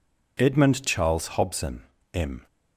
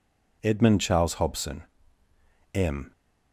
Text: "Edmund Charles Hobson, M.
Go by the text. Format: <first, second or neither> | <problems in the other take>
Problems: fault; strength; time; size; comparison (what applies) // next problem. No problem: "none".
neither | none